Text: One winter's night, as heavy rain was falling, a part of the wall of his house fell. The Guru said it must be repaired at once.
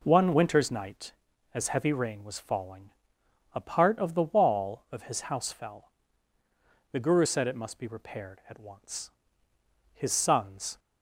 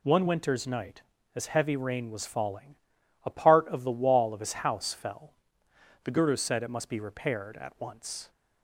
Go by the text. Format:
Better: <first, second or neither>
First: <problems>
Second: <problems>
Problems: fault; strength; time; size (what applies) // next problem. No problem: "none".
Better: second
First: goes on to say "His sons"; noticeable; from 9.9 s on; 0.86 s long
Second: none